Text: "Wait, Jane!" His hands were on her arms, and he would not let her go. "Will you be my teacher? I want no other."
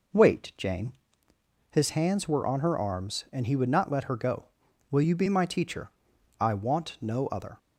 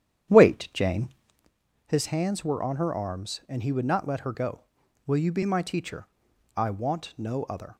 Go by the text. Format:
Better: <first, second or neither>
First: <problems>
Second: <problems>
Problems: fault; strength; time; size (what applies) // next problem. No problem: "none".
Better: first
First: none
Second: starts louder than the rest; strong; until 1.5 s; 9.5 dB